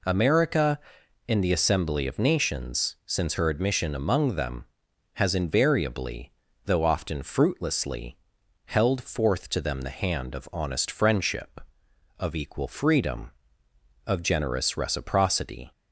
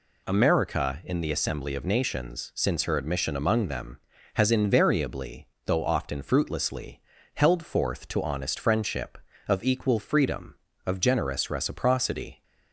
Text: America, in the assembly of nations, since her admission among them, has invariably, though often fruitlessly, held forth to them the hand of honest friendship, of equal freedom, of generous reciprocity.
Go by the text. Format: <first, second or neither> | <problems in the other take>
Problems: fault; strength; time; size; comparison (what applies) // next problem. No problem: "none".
first | skips "them the hand of"; at 8.2 s